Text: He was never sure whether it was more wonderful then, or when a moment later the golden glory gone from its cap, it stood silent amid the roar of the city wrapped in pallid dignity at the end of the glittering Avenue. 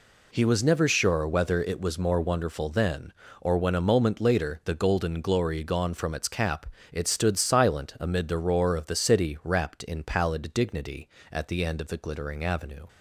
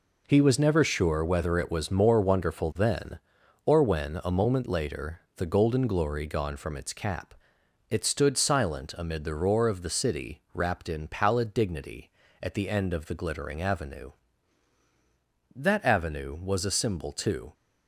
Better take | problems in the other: first | pauses between "later" and "the"; slight; at 5.2 s; 0.16 s long // goes on to say "That Avenue was a symbol too"; strong; from 15.5 s on; 1.9 s long

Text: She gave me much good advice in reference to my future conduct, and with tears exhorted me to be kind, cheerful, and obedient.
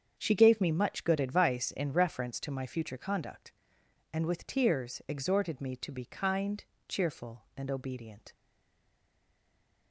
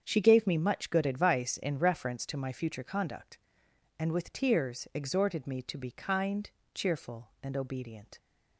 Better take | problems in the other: second | starts louder than the rest; strong; until 1.1 s; 7.5 dB; strong in the second // stays silent after the last word; noticeable; from 8.3 s on; 1.6 s long

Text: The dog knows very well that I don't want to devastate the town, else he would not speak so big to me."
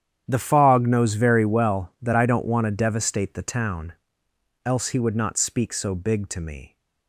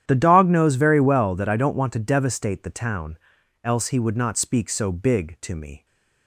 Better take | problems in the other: second | starts louder than the rest; strong; until 1.2 s; 9.5 dB; strong in the second // says "fog" for "dog"; at 0.3 s

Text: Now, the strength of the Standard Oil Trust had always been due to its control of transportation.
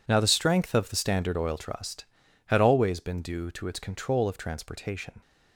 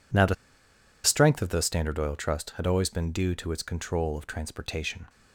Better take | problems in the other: first | pauses between "the" and "strength"; noticeable; at 0.3 s; 0.70 s long

